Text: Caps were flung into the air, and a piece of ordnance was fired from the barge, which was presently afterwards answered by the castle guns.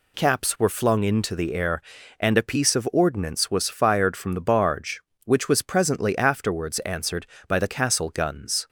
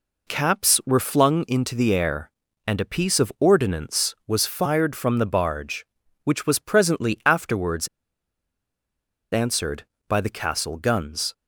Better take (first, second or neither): first